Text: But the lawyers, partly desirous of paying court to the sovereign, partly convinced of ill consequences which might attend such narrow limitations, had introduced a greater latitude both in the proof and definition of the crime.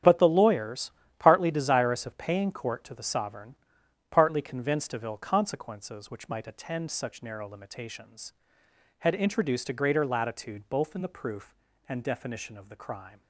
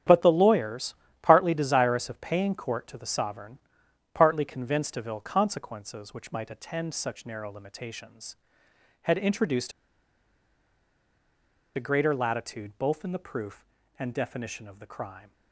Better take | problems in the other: first | starts louder than the rest; strong; until 1.3 s; 9.5 dB; strong in the first // pauses between "introduced" and "a"; strong; at 9.7 s; 2.0 s long

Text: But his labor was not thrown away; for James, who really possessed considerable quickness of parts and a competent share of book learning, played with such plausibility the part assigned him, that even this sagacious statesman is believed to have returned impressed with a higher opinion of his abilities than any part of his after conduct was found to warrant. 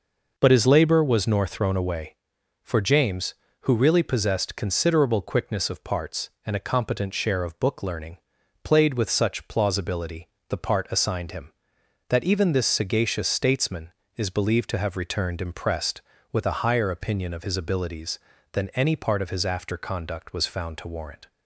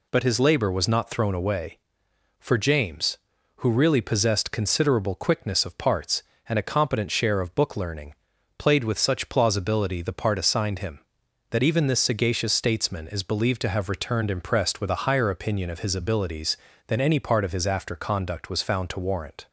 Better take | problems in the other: second | says "nor" for "not"; at 1.2 s // pauses between "plausibility" and "the"; slight; at 10.2 s; 0.20 s long

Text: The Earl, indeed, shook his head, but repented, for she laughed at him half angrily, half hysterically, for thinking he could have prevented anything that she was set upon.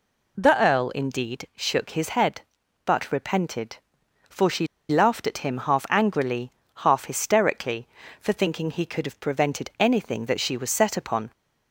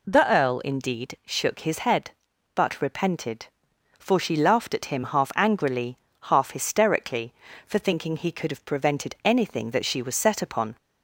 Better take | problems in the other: second | pauses between "she" and "laughed"; slight; at 4.6 s; 0.24 s long

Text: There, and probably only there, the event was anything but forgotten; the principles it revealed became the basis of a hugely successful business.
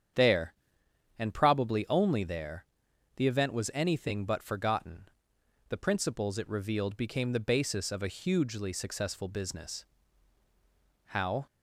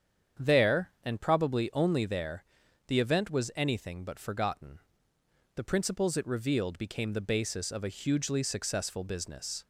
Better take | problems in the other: second | starts louder than the rest; strong; until 1.8 s; 8.5 dB; strong in the second // goes on to say "How"; slight; from 11.0 s on; 0.40 s long

